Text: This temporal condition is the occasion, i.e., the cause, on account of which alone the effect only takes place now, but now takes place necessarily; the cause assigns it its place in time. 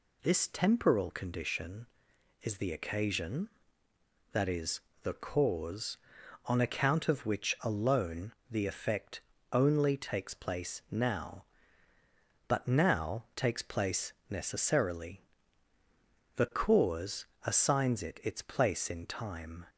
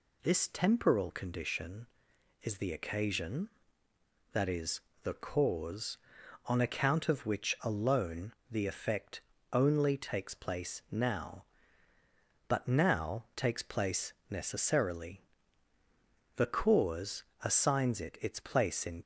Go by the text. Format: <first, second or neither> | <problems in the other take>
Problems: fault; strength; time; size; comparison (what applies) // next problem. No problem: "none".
first | pauses between "alone" and "the"; slight; at 8.3 s; 0.16 s long; slight in the first // pauses between "effect" and "only"; slight; at 9.2 s; 0.32 s long; slight in the first // pauses between "place" and "necessarily"; slight; at 14.1 s; 0.16 s long; slight in the first // pauses between "cause" and "assigns"; slight; at 17.2 s; 0.18 s long; slight in the first // stops before "time"; at 19.0 s